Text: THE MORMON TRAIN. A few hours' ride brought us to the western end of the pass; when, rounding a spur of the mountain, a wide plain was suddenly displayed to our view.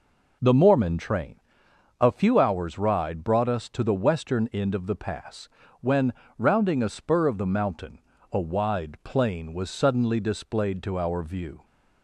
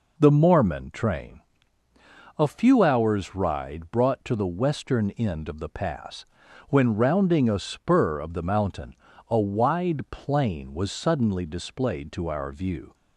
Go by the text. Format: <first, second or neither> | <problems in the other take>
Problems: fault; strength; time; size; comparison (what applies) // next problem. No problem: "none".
first | skips "us"; at 4.2 s